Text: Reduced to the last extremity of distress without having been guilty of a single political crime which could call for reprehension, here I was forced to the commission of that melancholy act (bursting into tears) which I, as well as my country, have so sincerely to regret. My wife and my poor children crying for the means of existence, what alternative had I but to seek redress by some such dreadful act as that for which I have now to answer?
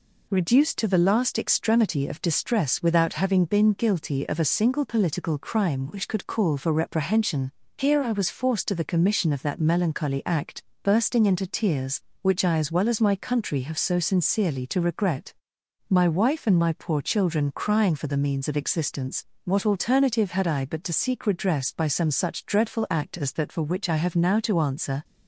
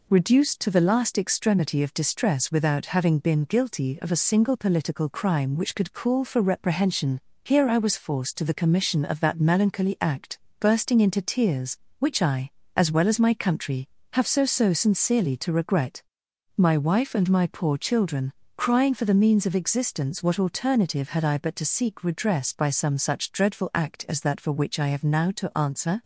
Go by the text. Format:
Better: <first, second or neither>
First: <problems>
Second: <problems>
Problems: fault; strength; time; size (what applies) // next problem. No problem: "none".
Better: first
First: none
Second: says "so" twice; at 14.4 s // pauses between "children" and "crying"; slight; at 18.3 s; 0.24 s long